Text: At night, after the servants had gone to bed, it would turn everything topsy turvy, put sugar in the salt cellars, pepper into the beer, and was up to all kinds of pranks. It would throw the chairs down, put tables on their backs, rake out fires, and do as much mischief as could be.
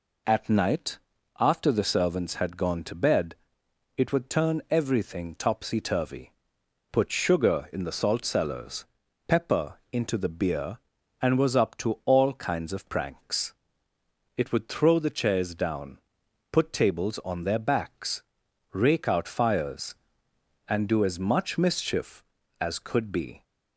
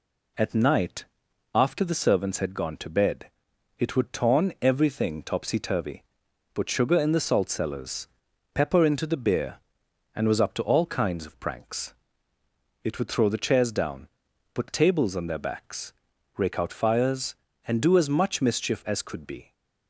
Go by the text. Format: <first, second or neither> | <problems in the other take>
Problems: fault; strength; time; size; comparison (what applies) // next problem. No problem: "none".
first | says "torn" for "turn"; at 4.1 s